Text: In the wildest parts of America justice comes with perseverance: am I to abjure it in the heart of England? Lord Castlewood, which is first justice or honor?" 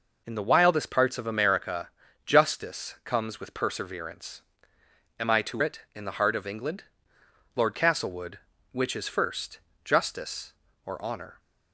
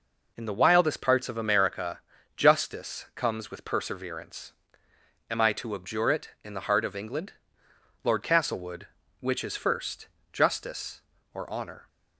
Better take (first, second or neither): second